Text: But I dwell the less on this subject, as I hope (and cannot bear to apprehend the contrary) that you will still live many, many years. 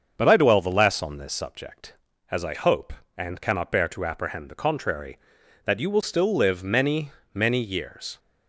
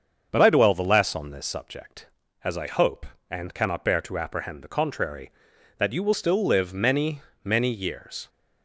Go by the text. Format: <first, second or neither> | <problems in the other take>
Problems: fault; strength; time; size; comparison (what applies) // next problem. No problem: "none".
neither | starts louder than the rest; the same in both